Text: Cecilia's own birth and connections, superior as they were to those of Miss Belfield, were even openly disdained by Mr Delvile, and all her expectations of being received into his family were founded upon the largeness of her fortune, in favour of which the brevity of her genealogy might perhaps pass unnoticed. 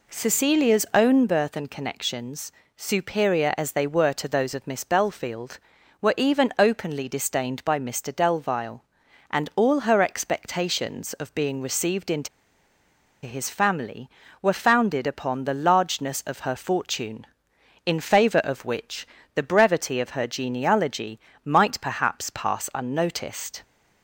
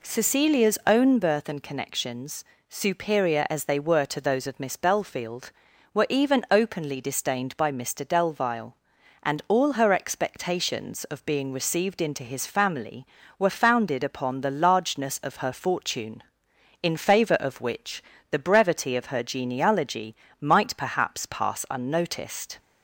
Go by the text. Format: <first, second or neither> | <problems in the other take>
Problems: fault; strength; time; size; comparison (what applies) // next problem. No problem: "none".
second | pauses between "into" and "his"; noticeable; at 12.2 s; 0.97 s long // pauses between "which" and "the"; slight; at 19.0 s; 0.28 s long; slight in the second // pauses between "genealogy" and "might"; slight; at 21.1 s; 0.24 s long; slight in the second